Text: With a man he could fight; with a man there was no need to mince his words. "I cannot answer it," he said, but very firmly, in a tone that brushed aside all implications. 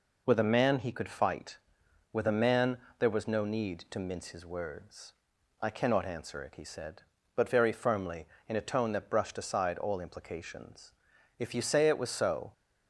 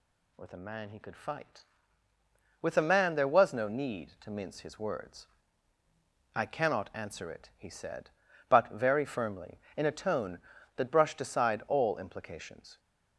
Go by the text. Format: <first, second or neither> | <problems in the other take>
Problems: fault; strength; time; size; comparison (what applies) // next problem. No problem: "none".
second | pauses between "man" and "there"; slight; at 2.7 s; 0.20 s long // goes on to say "If you say it was so"; noticeable; from 11.3 s on; 1.1 s long